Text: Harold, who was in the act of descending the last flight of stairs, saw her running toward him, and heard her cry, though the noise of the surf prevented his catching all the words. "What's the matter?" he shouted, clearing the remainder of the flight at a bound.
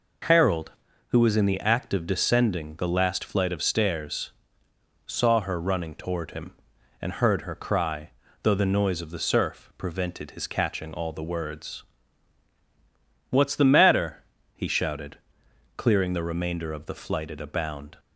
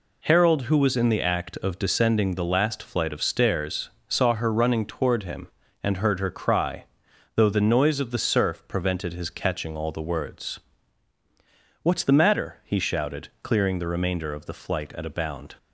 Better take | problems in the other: neither | none

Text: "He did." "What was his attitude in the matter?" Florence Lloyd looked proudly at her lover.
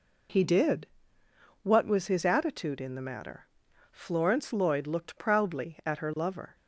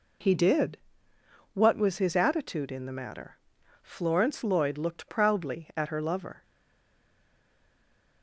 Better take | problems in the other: first | stays silent after the last word; noticeable; from 6.4 s on; 1.8 s long

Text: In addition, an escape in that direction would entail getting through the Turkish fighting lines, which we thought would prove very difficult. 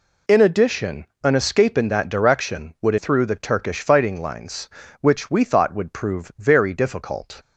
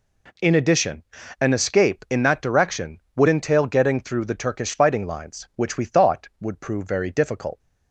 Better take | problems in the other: second | skips "entail getting"; at 2.9 s

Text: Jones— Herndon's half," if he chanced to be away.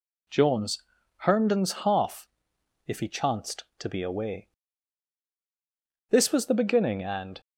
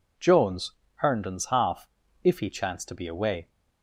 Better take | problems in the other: second | goes on to say "This was the beginning and"; noticeable; from 6.0 s on; 1.3 s long

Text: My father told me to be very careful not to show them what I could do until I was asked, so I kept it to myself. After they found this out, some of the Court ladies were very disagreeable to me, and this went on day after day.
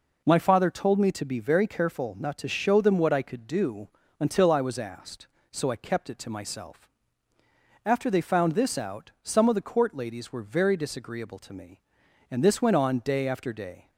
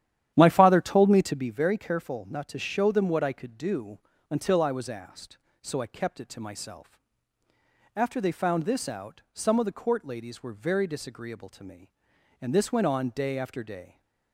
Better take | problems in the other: first | starts louder than the rest; strong; until 1.6 s; 11 dB // pauses between "do" and "until"; slight; at 3.9 s; 0.30 s long; slight in the first

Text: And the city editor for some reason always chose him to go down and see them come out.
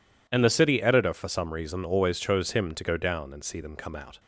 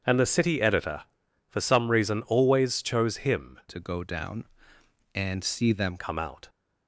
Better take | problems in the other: first | starts louder than the rest; until 1.5 s; 7 dB // changes voice from "to" to "them"; from 3.6 to 5.9 s; 2.3 s long

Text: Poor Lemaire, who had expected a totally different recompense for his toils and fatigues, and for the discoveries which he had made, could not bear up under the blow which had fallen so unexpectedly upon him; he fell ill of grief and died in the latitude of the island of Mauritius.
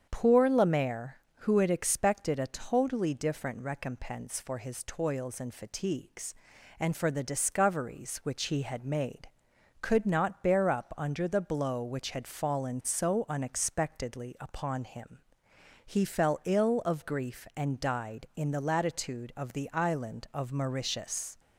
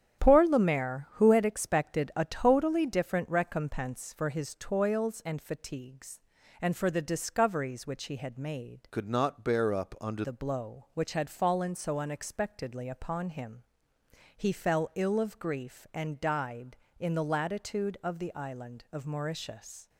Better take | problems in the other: first | starts louder than the rest; strong; until 1.2 s; 9 dB; strong in the first // changes voice from "could" to "under"; from 8.9 to 10.2 s; 1.3 s long

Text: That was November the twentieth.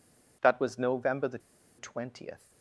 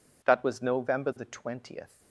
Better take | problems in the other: second | pauses between "the" and "twentieth"; at 1.3 s; 0.39 s long

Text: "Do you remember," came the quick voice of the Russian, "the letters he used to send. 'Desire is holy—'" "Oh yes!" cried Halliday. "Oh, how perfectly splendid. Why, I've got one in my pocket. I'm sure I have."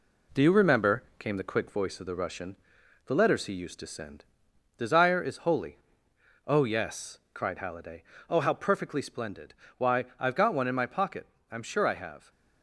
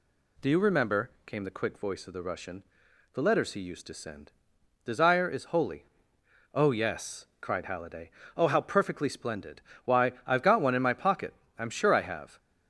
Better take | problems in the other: second | gets quieter; slight; throughout; 2.5 dB

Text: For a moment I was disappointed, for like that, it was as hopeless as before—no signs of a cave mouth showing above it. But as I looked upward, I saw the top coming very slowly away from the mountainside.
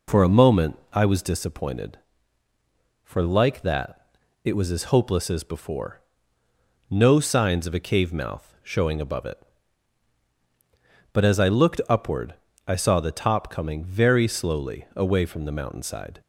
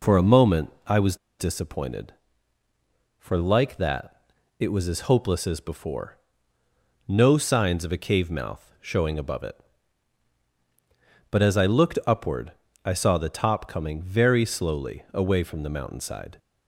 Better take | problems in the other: first | pauses between "was" and "disappointed"; slight; at 1.1 s; 0.24 s long

